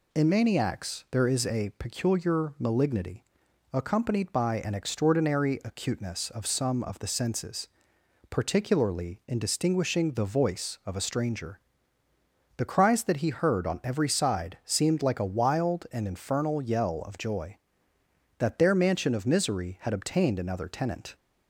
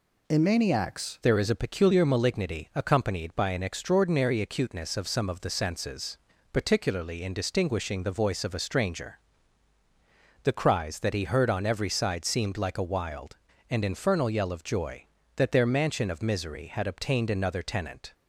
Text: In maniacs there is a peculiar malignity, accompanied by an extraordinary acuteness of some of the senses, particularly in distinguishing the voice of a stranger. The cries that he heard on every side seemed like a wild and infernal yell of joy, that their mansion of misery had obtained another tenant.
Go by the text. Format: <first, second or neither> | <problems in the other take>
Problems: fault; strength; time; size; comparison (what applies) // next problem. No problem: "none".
first | changes voice at "there"; from 1.2 s on; 16.9 s long